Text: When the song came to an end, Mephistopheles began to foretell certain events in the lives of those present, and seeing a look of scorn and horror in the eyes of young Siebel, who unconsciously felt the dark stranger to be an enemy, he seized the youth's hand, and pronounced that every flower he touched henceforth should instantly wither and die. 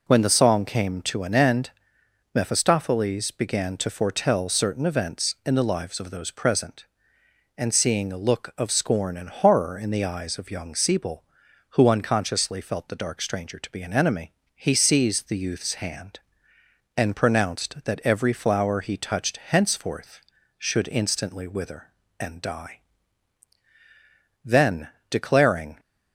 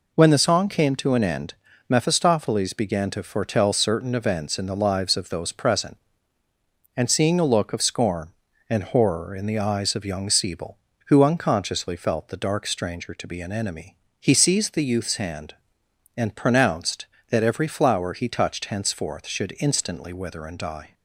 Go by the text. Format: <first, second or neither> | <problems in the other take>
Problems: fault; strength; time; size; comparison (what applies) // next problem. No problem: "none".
second | goes on to say "Then declaring"; from 24.4 s on; 1.3 s long